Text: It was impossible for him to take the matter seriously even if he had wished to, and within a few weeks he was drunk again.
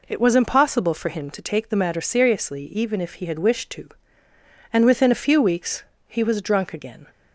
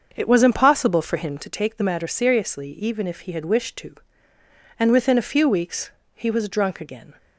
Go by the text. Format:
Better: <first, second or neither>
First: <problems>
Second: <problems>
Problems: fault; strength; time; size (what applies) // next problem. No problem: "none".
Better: first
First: pauses between "weeks" and "he"; slight; at 5.8 s; 0.24 s long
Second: starts louder than the rest; until 1.5 s; 6.5 dB // pauses between "weeks" and "he"; slight; at 5.9 s; 0.24 s long